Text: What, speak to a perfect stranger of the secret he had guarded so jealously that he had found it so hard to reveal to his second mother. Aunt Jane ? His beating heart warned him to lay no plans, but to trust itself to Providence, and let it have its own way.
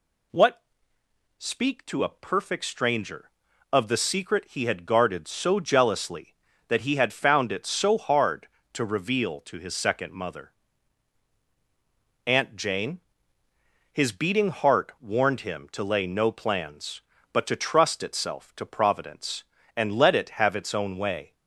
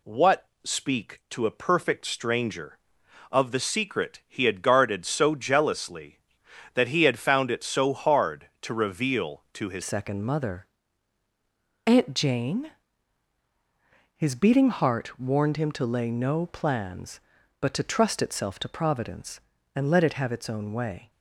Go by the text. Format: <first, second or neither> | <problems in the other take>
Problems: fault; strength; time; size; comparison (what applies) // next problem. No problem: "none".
first | changes voice at "second"; from 9.8 s on; 11.3 s long